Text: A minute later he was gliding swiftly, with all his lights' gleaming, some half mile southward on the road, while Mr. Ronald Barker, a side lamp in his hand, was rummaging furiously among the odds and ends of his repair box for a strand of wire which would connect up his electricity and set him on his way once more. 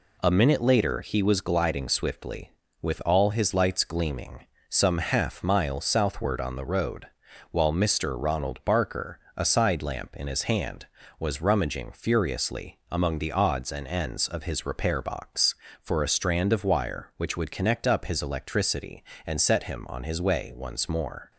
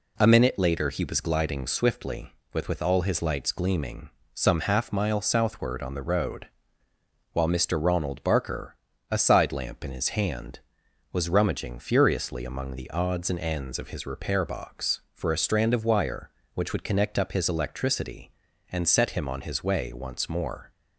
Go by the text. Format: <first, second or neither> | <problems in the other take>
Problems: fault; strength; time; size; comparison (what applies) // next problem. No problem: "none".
first | says "with" twice; at 2.6 s